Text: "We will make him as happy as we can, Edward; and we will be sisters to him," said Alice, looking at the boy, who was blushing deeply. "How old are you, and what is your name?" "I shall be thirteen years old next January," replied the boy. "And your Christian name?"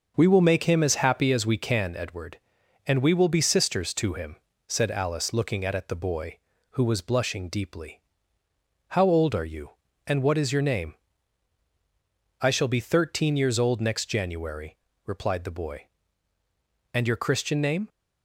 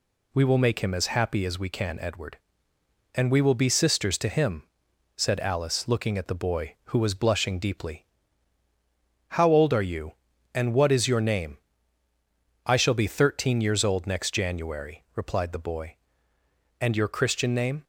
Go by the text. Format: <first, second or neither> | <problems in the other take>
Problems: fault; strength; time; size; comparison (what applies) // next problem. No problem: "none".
second | starts louder than the rest; noticeable; until 1.1 s; 6 dB // says "at" twice; at 5.7 s